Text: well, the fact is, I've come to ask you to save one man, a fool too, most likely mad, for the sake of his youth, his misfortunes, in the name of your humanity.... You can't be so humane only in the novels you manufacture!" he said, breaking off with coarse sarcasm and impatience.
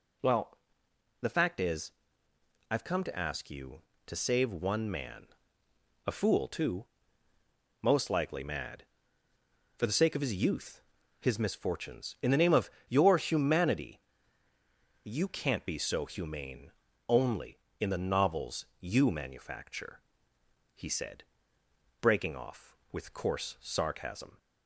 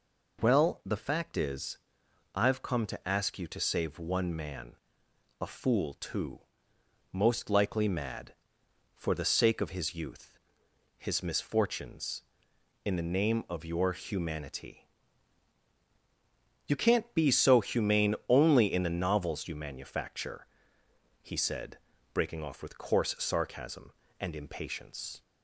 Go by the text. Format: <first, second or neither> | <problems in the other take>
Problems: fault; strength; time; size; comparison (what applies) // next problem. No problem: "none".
second | pauses between "of" and "your"; slight; at 12.6 s; 0.18 s long // pauses between "humane" and "only"; at 16.6 s; 0.38 s long // pauses between "novels" and "you"; slight; at 18.6 s; 0.16 s long // stops before "and impatience"; at 24.3 s